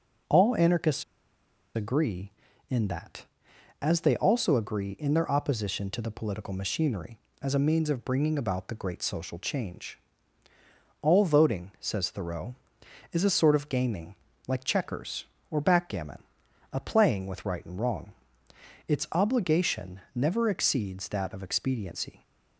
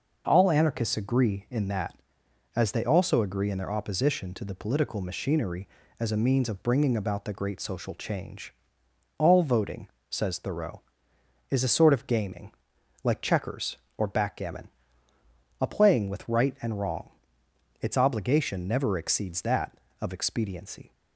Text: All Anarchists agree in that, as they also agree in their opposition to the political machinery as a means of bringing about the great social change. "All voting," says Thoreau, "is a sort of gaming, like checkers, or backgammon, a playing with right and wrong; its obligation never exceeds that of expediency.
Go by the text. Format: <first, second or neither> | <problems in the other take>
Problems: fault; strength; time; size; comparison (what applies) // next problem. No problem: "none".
second | pauses between "Anarchists" and "agree"; noticeable; at 1.0 s; 0.72 s long